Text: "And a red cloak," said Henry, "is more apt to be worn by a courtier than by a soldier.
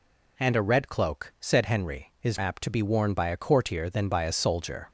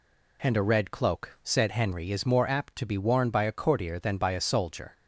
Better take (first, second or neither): second